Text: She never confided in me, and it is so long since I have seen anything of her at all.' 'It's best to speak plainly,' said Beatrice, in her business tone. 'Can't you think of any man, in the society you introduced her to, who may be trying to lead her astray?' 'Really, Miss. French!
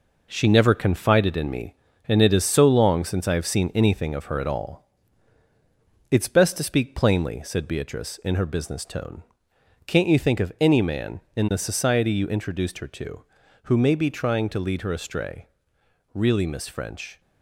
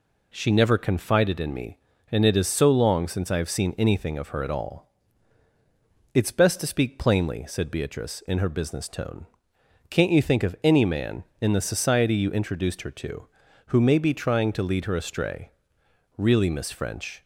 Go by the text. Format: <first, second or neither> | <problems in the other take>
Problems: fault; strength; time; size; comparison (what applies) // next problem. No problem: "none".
second | gets quieter; throughout; 6.5 dB